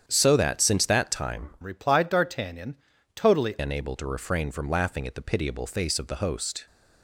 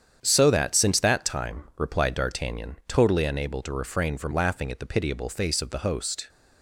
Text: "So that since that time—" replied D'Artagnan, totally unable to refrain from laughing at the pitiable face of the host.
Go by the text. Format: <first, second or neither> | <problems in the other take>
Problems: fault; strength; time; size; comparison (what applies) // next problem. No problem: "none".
second | starts louder than the rest; strong; until 1.0 s; 8.5 dB; strong in the second // changes voice from "replied" to "totally"; from 1.6 to 3.5 s; 1.9 s long